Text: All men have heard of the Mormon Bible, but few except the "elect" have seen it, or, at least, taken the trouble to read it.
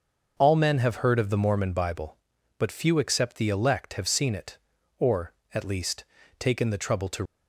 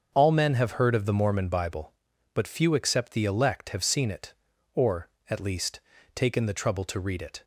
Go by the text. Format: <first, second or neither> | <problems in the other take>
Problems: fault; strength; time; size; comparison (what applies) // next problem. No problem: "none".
second | starts louder than the rest; until 1.3 s; 6 dB; also in the second // stops before "read it"; at 7.2 s